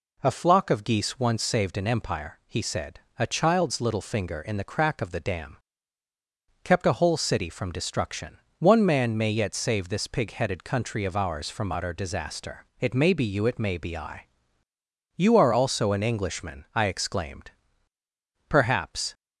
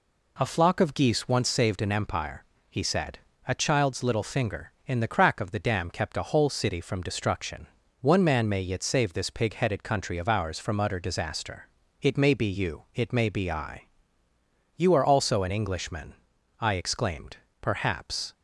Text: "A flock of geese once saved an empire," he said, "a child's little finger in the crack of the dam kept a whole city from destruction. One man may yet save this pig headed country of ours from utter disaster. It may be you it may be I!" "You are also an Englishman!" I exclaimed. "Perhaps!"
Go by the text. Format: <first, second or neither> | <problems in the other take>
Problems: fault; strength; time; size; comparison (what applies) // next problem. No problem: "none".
second | pauses between "dam" and "kept"; at 5.5 s; 1.0 s long